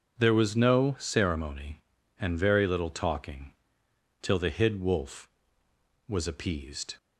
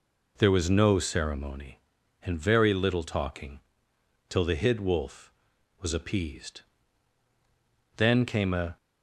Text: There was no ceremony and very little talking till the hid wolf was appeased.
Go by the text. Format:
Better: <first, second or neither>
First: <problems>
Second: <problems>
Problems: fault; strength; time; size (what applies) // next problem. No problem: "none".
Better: first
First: pauses between "talking" and "till"; noticeable; at 3.5 s; 0.70 s long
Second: pauses between "talking" and "till"; noticeable; at 3.6 s; 0.68 s long // goes on to say "Then came a"; noticeable; from 7.9 s on; 0.80 s long